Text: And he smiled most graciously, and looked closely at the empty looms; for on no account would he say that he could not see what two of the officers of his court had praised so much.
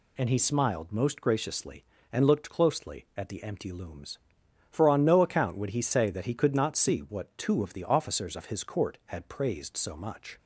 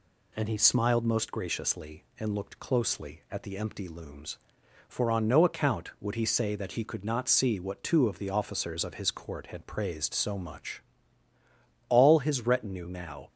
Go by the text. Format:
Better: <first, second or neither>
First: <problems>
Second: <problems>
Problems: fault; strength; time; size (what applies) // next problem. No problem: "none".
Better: first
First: none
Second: goes on to say "All his retinue now"; from 11.8 s on; 1.4 s long